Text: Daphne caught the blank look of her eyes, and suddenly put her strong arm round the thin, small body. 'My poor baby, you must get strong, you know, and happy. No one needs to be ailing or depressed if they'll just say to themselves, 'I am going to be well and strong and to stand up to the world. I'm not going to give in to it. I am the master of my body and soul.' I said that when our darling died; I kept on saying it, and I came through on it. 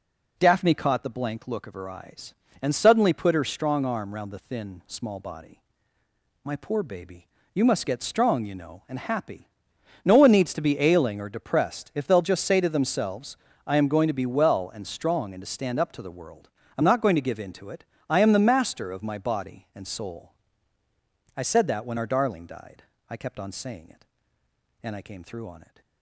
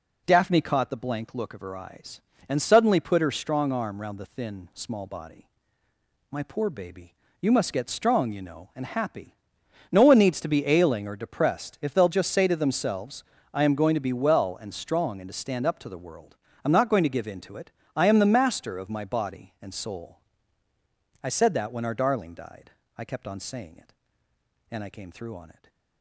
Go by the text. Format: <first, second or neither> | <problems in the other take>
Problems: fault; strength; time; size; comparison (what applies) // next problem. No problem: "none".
neither | none